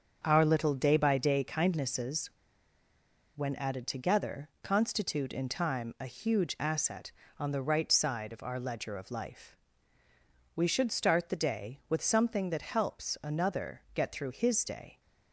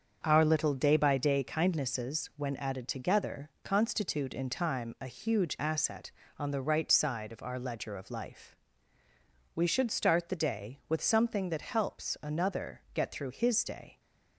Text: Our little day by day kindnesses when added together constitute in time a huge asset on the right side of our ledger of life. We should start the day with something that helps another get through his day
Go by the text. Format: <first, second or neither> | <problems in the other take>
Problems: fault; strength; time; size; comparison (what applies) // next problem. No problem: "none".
second | starts louder than the rest; until 1.2 s; 6.5 dB; also in the second // pauses between "kindnesses" and "when"; at 2.3 s; 1.0 s long // pauses between "together" and "constitute"; slight; at 4.4 s; 0.16 s long; slight in the second